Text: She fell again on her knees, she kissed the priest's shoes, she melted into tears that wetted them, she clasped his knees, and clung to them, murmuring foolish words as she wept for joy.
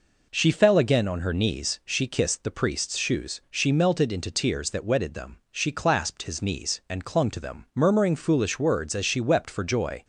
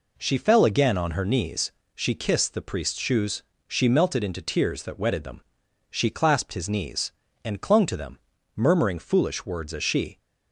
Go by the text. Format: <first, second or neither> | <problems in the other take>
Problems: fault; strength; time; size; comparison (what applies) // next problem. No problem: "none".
first | stops before "wept for joy"; at 10.1 s